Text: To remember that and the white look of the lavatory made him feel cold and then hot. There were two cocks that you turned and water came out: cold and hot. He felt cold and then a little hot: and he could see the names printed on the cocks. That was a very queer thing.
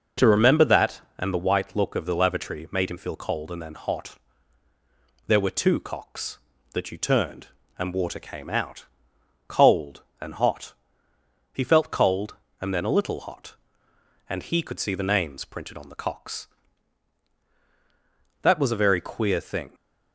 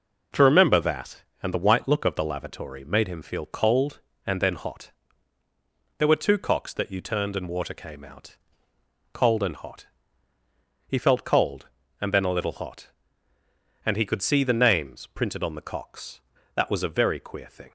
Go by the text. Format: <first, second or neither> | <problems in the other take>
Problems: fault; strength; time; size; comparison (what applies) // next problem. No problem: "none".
neither | none